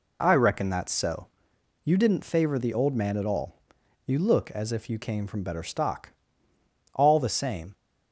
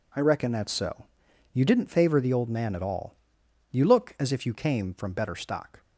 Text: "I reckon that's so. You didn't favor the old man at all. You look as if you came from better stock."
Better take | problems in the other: second | goes on to say "All the same"; noticeable; from 6.9 s on; 0.80 s long

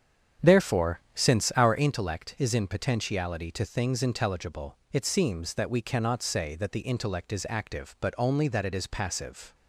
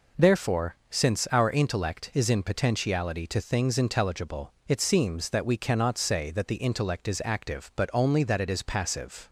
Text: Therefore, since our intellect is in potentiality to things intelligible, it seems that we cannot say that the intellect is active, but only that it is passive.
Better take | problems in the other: second | starts louder than the rest; strong; until 1.9 s; 8 dB

